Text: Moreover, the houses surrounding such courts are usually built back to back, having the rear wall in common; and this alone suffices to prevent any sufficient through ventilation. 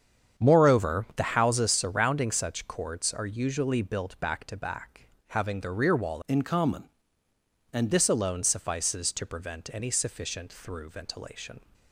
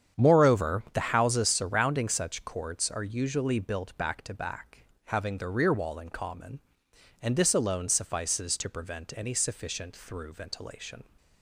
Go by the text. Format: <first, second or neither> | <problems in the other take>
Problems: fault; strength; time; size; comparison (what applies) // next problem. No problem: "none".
second | starts louder than the rest; strong; until 1.4 s; 8 dB; strong in the second // changes voice from "in" to "and"; from 6.2 to 7.9 s; 1.7 s long